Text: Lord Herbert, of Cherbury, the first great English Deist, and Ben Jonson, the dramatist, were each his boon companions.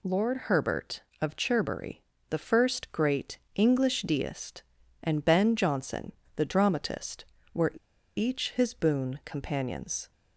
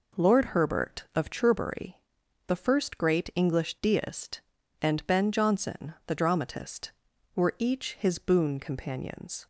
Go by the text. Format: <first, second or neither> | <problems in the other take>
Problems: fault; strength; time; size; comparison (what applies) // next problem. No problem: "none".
second | pauses between "great" and "English"; slight; at 3.3 s; 0.18 s long // pauses between "were" and "each"; at 7.7 s; 0.42 s long